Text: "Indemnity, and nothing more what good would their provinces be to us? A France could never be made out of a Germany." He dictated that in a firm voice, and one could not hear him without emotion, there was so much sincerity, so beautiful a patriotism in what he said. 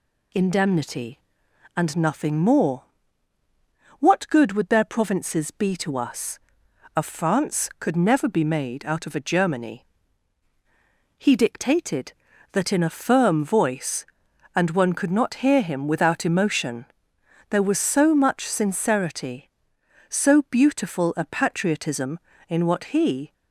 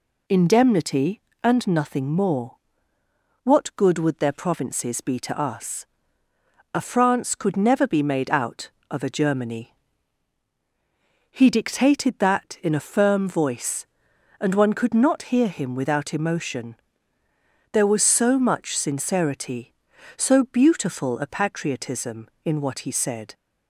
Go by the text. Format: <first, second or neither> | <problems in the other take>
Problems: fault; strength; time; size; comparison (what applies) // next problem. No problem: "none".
second | pauses between "more" and "what"; at 2.8 s; 1.1 s long; noticeable in the second // stops before "said"; at 23.3 s